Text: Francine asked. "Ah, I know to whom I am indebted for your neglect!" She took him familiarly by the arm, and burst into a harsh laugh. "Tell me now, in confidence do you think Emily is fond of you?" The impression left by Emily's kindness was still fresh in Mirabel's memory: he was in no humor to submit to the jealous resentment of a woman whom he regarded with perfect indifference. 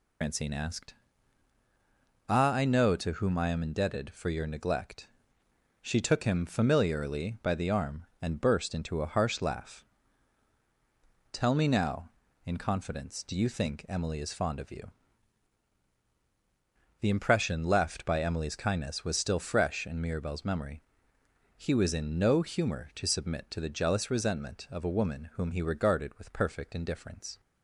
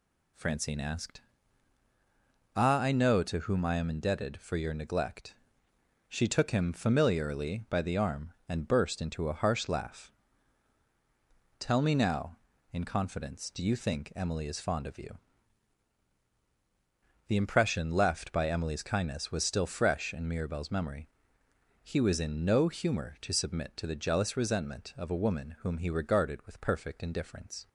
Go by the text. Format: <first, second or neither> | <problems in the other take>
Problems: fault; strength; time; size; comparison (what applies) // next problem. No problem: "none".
second | loses the start of "Francine"; at 0.2 s; 130 ms